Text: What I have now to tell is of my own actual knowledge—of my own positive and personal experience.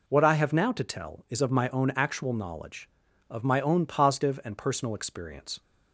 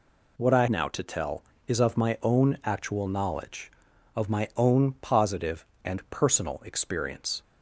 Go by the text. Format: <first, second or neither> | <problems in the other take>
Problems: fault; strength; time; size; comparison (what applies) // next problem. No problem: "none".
first | skips "have"; at 0.6 s